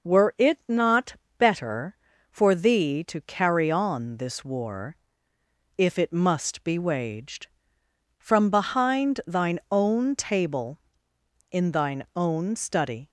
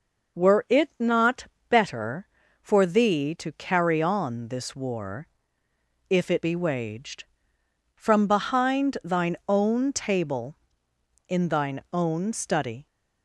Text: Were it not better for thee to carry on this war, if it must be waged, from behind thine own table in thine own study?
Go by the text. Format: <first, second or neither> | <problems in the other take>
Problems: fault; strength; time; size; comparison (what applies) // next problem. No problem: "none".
first | pauses between "not" and "better"; slight; at 1.4 s; 0.24 s long; slight in the first // skips "must"; at 6.4 s